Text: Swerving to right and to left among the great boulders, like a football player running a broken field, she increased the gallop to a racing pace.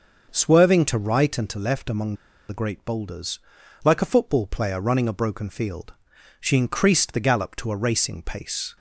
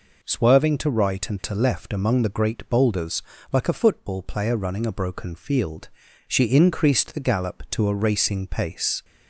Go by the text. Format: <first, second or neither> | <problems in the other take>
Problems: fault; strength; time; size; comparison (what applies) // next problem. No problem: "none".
second | pauses between "among" and "the"; slight; at 2.1 s; 0.34 s long